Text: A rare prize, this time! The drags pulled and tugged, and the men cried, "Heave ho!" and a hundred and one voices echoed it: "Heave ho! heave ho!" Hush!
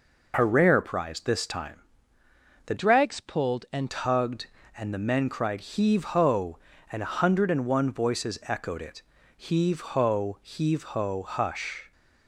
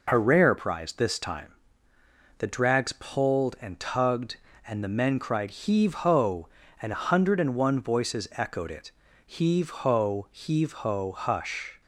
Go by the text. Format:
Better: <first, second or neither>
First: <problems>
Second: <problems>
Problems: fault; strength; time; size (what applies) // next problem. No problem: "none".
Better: second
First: changes voice from "drags" to "and"; from 2.7 to 3.9 s; 1.2 s long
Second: none